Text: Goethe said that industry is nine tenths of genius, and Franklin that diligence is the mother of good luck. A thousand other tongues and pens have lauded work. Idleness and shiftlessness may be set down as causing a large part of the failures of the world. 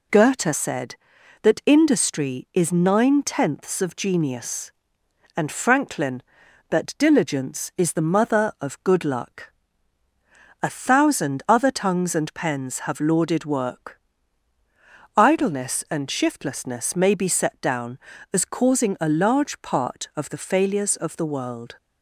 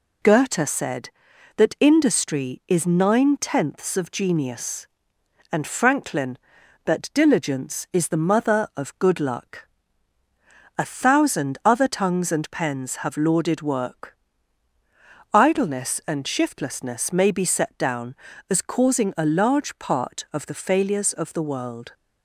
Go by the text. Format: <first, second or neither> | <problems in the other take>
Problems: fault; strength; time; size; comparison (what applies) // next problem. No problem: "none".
neither | none